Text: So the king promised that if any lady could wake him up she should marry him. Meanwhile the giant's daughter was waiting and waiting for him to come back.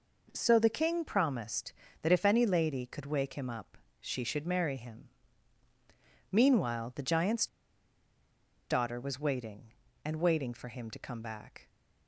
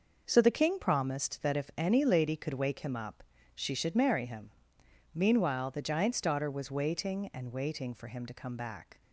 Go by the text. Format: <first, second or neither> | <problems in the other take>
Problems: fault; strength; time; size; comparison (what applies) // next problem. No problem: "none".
second | pauses between "up" and "she"; slight; at 3.7 s; 0.24 s long; slight in the second // pauses between "giant's" and "daughter"; at 7.4 s; 1.2 s long